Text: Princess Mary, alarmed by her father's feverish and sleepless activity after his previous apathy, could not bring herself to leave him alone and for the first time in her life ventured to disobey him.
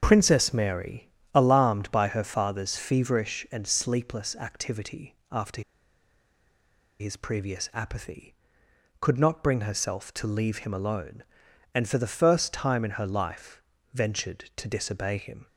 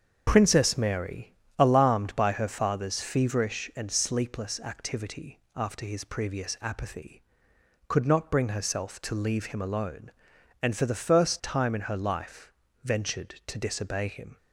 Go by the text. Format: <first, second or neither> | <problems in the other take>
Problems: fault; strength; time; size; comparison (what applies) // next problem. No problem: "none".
second | starts louder than the rest; until 1.0 s; 7 dB; also in the second // pauses between "activity" and "after"; slight; at 5.1 s; 0.16 s long; slight in the second // pauses between "after" and "his"; strong; at 5.6 s; 1.3 s long // pauses between "life" and "ventured"; slight; at 13.6 s; 0.32 s long; slight in the second